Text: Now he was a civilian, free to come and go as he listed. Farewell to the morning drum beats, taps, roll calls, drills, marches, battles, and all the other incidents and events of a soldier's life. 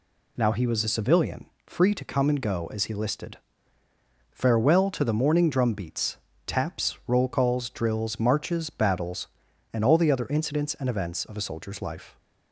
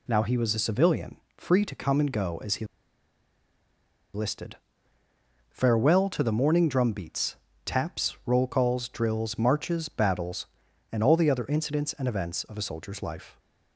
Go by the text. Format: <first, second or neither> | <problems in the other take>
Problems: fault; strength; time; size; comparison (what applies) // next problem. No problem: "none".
first | pauses between "he" and "listed"; strong; at 2.6 s; 1.4 s long